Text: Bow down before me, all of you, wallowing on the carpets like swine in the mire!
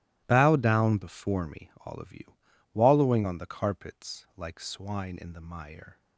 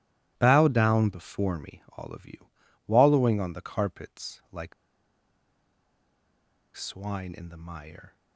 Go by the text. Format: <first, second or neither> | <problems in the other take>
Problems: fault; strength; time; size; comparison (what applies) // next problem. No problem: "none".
first | starts louder than the rest; strong; until 1.3 s; 16 dB; strong in the first // pauses between "like" and "swine"; strong; at 4.7 s; 2.0 s long